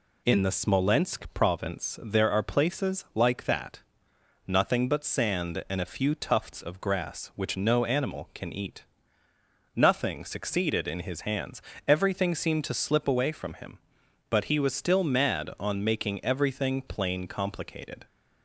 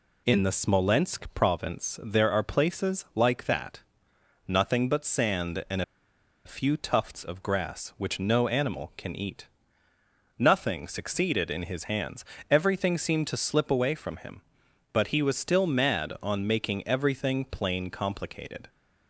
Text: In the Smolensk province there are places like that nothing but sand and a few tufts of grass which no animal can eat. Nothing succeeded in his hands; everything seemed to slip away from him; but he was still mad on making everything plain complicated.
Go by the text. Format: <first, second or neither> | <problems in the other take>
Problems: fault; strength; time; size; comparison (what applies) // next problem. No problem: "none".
first | pauses between "that" and "nothing"; noticeable; at 3.8 s; 0.66 s long; noticeable in the first // pauses between "and" and "a"; noticeable; at 5.8 s; 0.63 s long